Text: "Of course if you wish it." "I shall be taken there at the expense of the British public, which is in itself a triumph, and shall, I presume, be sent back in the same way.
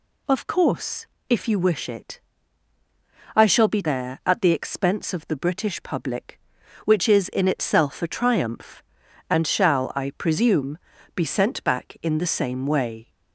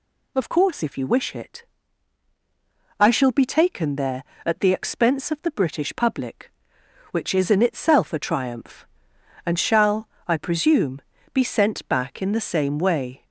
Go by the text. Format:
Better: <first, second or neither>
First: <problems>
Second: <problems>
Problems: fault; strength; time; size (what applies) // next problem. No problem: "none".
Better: second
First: pauses between "course" and "if"; slight; at 1.0 s; 0.24 s long // skips "taken"; at 3.8 s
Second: none